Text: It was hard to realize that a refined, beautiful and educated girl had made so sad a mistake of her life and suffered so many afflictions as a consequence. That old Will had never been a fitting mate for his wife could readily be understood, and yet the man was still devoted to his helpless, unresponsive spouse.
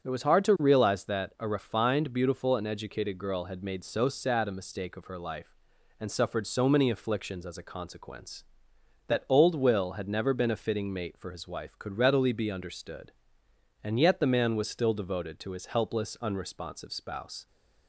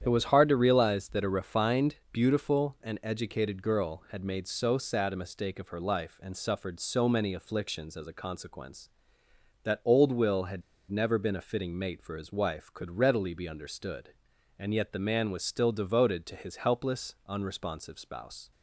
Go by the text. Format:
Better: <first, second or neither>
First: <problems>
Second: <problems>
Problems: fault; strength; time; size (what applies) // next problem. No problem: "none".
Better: first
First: starts louder than the rest; strong; until 1.1 s; 8 dB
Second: starts louder than the rest; strong; until 1.0 s; 9 dB // pauses between "had" and "never"; slight; at 10.6 s; 0.28 s long